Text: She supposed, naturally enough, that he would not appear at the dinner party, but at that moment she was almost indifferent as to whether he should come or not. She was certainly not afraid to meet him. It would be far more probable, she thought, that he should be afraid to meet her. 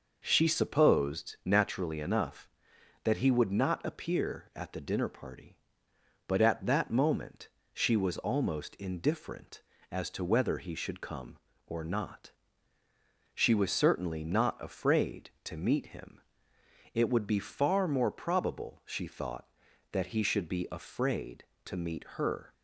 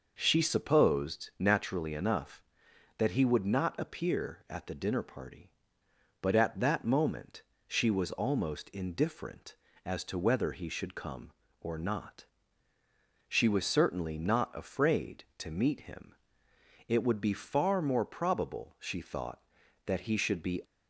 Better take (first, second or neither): first